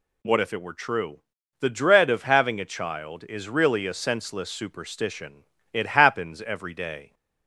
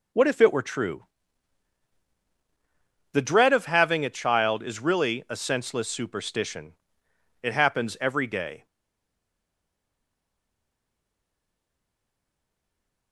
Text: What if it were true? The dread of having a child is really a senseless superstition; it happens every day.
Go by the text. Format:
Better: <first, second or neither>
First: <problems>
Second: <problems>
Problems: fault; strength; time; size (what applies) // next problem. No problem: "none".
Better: first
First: none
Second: stays silent after the last word; strong; from 8.6 s on; 4.5 s long